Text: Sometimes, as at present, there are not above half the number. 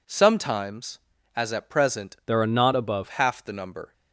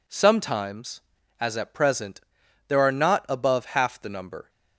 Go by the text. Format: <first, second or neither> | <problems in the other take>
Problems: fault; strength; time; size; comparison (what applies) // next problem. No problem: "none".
second | changes voice from "there" to "above"; from 2.2 to 3.0 s; 0.8 s long